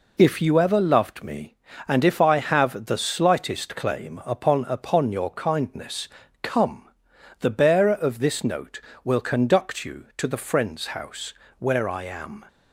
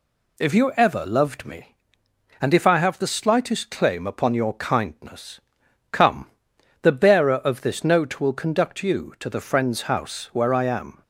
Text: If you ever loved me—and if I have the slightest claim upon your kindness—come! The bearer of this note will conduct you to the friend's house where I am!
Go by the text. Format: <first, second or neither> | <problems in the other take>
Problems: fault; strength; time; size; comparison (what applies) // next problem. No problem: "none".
second | says "upon" twice; at 4.6 s // pauses between "house" and "where"; slight; at 11.3 s; 0.24 s long